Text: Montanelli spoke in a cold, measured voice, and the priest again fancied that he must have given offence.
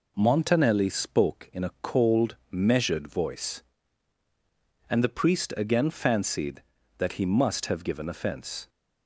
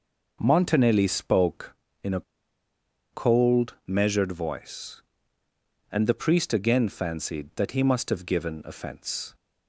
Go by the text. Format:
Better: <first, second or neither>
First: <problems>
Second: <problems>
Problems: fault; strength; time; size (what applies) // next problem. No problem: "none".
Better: first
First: none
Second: pauses between "a" and "cold"; noticeable; at 2.2 s; 0.91 s long